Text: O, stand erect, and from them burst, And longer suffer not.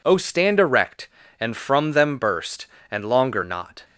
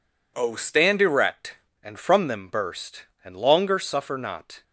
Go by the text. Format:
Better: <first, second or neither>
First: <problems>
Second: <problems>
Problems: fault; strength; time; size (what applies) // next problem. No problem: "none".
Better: second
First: skips "suffer"; at 3.4 s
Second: none